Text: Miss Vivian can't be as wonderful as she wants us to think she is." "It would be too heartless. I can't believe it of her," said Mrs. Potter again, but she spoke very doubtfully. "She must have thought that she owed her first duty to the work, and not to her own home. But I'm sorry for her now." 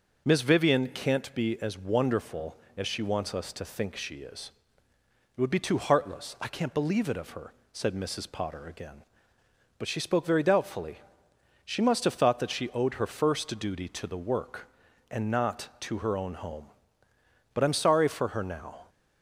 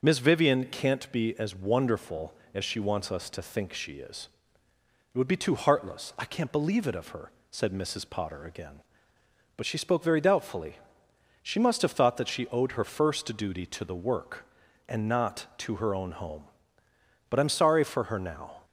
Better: neither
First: starts louder than the rest; noticeable; until 1.2 s; 6 dB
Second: starts louder than the rest; until 1.0 s; 6.5 dB

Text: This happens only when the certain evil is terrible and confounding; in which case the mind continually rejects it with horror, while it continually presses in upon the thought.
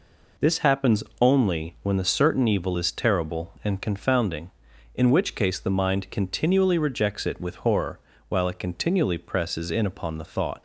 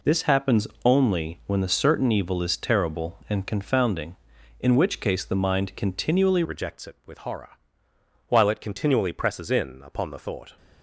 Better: first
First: pauses between "happens" and "only"; slight; at 1.0 s; 0.16 s long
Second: pauses between "happens" and "only"; slight; at 0.6 s; 0.16 s long // changes voice at "rejects"; from 6.4 s on; 4.1 s long

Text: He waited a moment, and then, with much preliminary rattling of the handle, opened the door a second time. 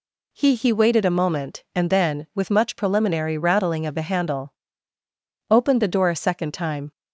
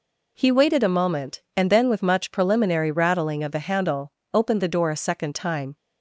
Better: second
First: says "He" twice; at 0.5 s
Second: none

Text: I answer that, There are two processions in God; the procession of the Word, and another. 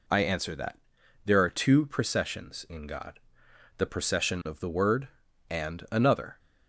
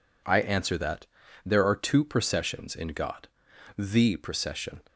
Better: first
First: none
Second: stops before "of the Word and another"; at 4.8 s

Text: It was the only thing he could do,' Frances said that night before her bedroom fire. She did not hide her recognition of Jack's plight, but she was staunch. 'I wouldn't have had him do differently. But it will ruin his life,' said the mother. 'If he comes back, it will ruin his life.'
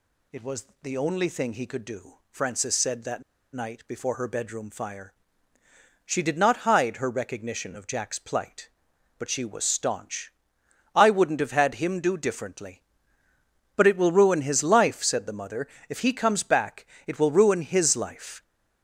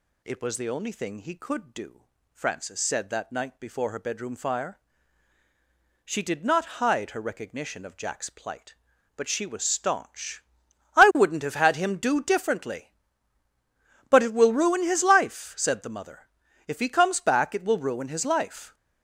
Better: second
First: pauses between "was" and "the"; slight; at 0.6 s; 0.18 s long // pauses between "that" and "night"; slight; at 3.2 s; 0.30 s long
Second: none

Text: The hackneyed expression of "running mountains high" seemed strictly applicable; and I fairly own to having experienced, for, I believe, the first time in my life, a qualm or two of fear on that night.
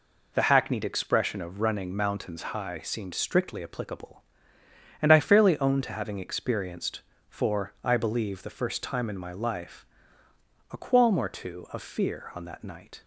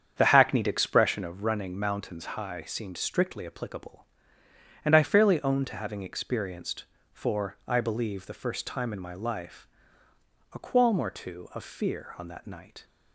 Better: first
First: none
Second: starts louder than the rest; strong; until 1.4 s; 8 dB

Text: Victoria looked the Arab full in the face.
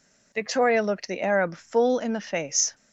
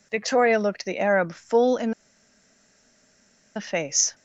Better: first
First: none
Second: pauses between "in" and "the"; strong; at 1.9 s; 1.6 s long

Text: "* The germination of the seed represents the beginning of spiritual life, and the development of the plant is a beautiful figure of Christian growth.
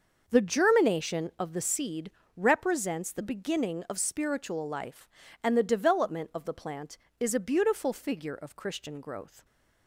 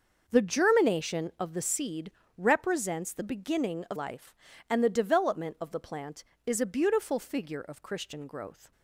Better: first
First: starts louder than the rest; noticeable; until 1.2 s; 6 dB // pauses between "seed" and "represents"; slight; at 2.1 s; 0.23 s long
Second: starts louder than the rest; noticeable; until 1.2 s; 6 dB // pauses between "seed" and "represents"; slight; at 2.1 s; 0.24 s long // skips "spiritual"; at 3.9 s

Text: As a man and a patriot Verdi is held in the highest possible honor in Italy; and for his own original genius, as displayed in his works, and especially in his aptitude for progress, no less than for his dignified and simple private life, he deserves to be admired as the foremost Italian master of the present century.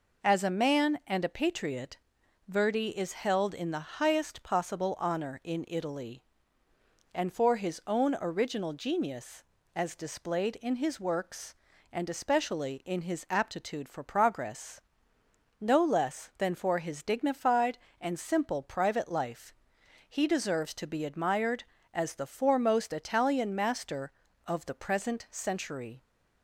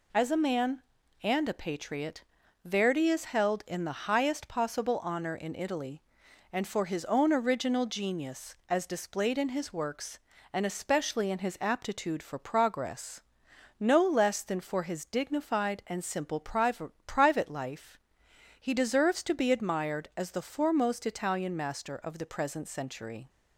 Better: first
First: pauses between "patriot" and "Verdi"; noticeable; at 1.9 s; 0.50 s long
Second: pauses between "patriot" and "Verdi"; at 2.2 s; 0.42 s long // says "private" twice; at 17.0 s

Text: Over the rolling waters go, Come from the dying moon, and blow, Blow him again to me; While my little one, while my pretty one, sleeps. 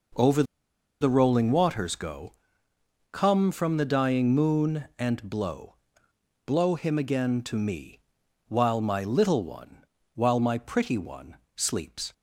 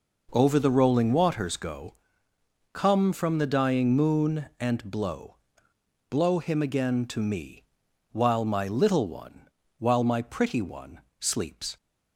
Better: second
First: pauses between "Over" and "the"; noticeable; at 0.4 s; 0.57 s long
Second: none

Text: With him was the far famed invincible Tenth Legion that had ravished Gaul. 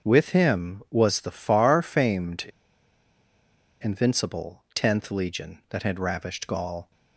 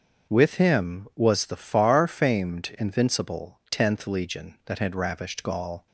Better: second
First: starts louder than the rest; until 1.1 s; 6.5 dB // pauses between "famed" and "invincible"; strong; at 2.4 s; 1.3 s long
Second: starts louder than the rest; until 1.3 s; 6.5 dB

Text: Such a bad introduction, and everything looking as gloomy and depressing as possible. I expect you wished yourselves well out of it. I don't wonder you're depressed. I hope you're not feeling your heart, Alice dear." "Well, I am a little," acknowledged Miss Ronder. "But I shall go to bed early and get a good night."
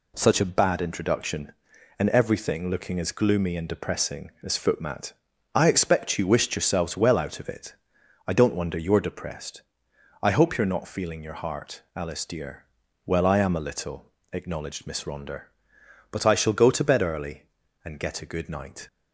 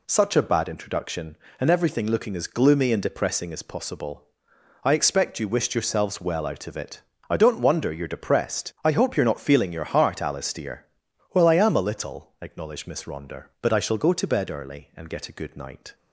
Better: second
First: says "footmat" for "possible"; at 4.5 s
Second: none

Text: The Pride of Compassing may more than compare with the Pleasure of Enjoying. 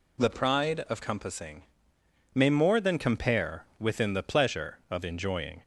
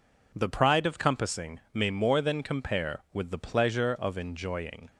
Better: second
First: pauses between "Compassing" and "may"; noticeable; at 1.6 s; 0.72 s long // says "within" for "with"; at 3.7 s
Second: pauses between "Compassing" and "may"; slight; at 1.5 s; 0.16 s long

